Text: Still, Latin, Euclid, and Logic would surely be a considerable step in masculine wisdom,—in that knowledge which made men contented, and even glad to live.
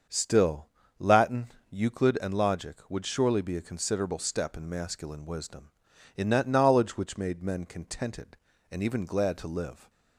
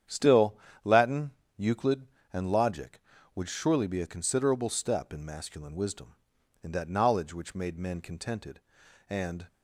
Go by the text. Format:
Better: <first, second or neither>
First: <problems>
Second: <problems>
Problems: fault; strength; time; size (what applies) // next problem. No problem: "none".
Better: first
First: starts louder than the rest; until 1.4 s; 6.5 dB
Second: starts louder than the rest; strong; until 1.6 s; 9 dB // stops before "even glad to live"; at 9.4 s